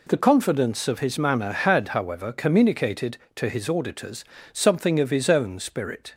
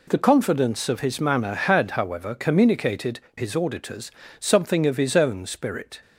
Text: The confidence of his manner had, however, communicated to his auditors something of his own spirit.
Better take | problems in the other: first | skips "to"; at 3.2 s // pauses between "auditors" and "something"; slight; at 4.1 s; 0.28 s long; slight in the first

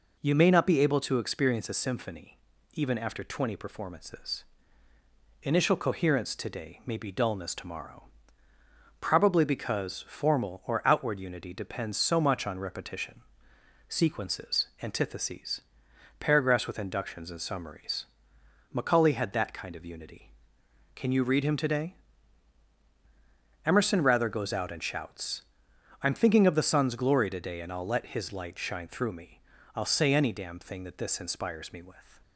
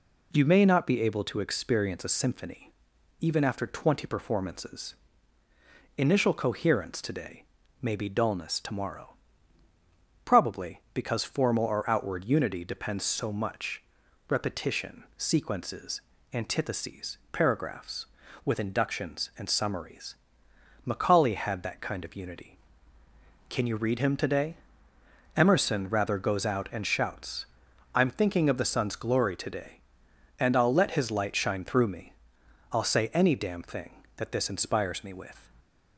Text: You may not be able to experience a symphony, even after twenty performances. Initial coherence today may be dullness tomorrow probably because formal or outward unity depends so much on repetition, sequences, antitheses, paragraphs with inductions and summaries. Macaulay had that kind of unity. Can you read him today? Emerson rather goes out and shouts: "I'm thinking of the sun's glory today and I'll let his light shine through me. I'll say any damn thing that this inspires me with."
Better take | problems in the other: first | pauses between "today" and "may"; at 7.4 s; 0.38 s long // pauses between "tomorrow" and "probably"; at 9.0 s; 1.1 s long; noticeable in the first // skips "on"; at 14.0 s

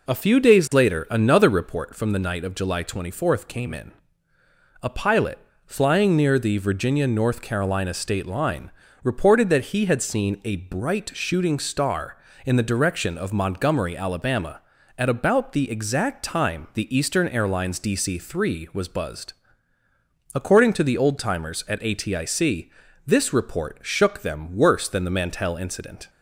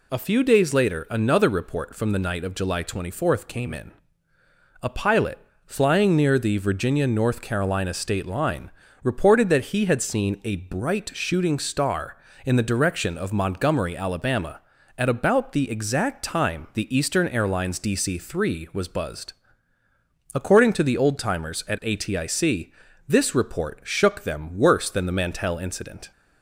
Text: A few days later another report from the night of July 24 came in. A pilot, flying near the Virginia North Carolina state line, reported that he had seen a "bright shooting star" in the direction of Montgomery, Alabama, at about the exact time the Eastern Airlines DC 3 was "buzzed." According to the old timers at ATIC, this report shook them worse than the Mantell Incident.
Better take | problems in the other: second | starts louder than the rest; noticeable; until 1.7 s; 4 dB

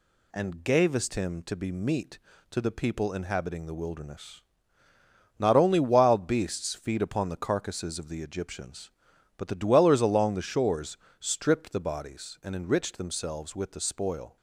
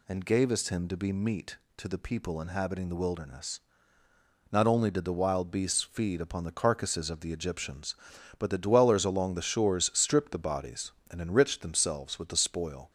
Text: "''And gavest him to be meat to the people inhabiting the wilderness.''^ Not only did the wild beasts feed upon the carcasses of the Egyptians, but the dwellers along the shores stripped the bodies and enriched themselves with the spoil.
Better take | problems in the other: second | skips "did the"; at 5.8 s // pauses between "shores" and "stripped"; slight; at 10.9 s; 0.20 s long

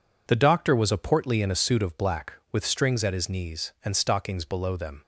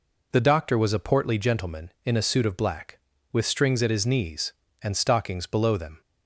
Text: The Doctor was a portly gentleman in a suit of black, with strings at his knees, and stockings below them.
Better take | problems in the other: second | skips "gentleman"; at 1.4 s

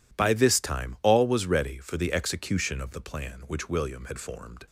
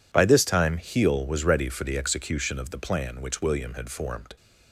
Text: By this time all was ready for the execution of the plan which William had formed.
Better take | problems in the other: first | says "heel" for "all"; at 0.7 s

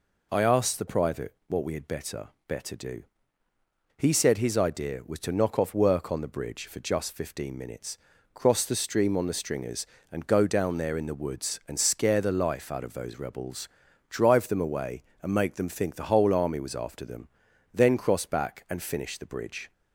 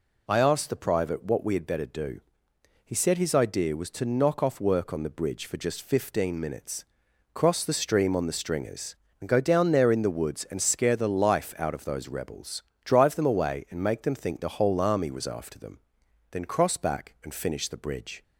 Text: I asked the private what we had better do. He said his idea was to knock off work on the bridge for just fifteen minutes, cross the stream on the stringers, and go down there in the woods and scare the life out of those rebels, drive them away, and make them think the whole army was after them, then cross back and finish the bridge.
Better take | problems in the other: second | says "better" twice; at 2.4 s

